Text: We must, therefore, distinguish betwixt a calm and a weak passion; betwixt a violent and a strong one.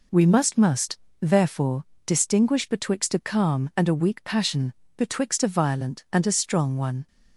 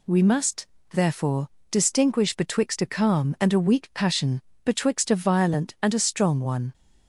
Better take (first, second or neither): second